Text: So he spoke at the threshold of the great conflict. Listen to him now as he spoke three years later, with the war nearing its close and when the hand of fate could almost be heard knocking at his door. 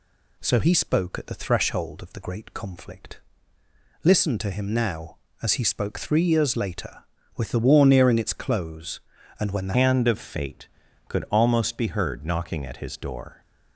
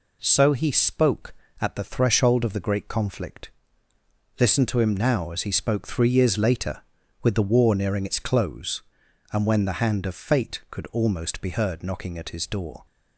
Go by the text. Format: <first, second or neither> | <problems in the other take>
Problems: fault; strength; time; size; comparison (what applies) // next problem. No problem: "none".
second | changes voice at "hand"; from 9.7 s on; 3.7 s long